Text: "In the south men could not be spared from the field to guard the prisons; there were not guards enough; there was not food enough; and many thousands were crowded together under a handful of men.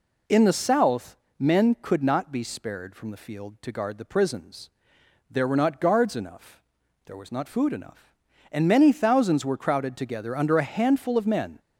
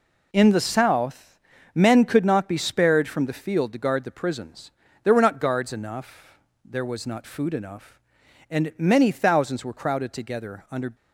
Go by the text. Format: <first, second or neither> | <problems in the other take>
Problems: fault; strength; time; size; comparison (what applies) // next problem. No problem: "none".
first | pauses between "south" and "men"; slight; at 1.3 s; 0.34 s long; slight in the first // stops before "a handful of men"; at 10.9 s